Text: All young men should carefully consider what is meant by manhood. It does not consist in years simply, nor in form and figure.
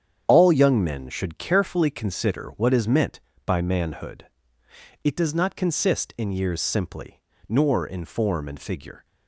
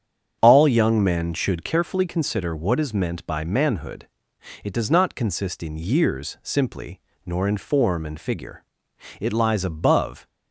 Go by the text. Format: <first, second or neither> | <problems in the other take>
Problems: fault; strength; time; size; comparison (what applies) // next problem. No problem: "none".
first | starts louder than the rest; strong; until 1.4 s; 8 dB; strong in the first // goes on to say "It lies above"; noticeable; from 9.1 s on; 1.1 s long